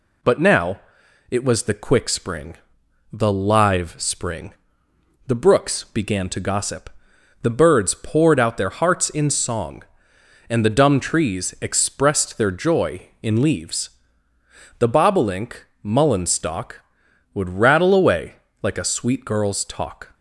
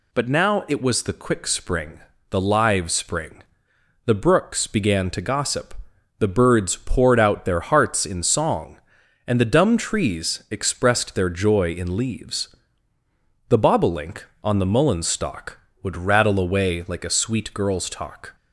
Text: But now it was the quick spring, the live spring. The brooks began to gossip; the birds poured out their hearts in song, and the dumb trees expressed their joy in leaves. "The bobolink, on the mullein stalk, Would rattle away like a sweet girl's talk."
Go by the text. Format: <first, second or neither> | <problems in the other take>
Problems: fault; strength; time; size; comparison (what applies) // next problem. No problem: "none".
second | pauses between "now" and "it"; noticeable; at 0.7 s; 0.50 s long // skips "on the"; at 15.7 s // pauses between "away" and "like"; slight; at 18.3 s; 0.26 s long